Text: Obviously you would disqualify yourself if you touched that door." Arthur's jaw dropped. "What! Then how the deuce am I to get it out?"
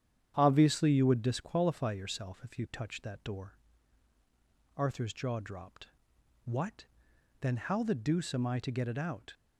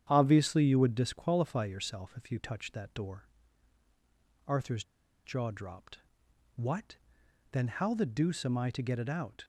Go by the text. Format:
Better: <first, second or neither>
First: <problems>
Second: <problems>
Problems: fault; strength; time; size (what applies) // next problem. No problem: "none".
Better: first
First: starts louder than the rest; strong; until 1.3 s; 9.5 dB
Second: starts louder than the rest; strong; until 1.1 s; 9.5 dB // pauses between "Arthur's" and "jaw"; at 4.8 s; 0.43 s long